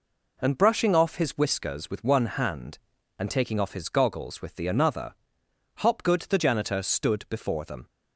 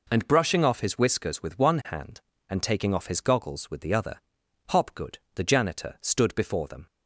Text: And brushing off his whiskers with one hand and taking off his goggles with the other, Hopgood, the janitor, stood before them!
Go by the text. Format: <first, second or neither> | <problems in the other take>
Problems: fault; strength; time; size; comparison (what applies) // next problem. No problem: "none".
second | says "another" for "other"; at 4.6 s